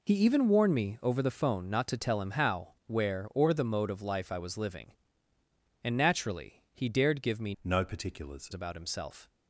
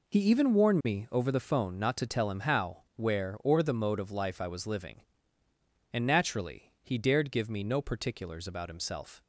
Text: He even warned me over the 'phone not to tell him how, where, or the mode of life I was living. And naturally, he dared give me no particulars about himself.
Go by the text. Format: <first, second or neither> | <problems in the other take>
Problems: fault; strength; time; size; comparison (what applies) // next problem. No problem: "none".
second | changes voice from "no" to "particulars"; from 7.6 to 8.5 s; 0.9 s long